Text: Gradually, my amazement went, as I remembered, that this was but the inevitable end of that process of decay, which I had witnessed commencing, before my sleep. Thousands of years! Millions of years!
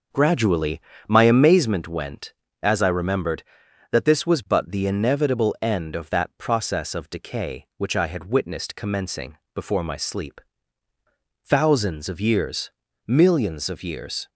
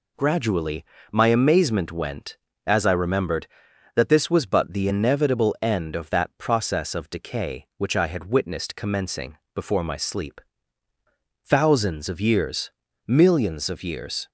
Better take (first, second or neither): second